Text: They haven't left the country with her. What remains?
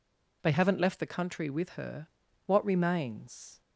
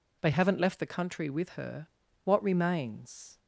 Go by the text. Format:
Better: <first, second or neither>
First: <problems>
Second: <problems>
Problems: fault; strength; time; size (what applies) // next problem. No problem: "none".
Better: neither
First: none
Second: none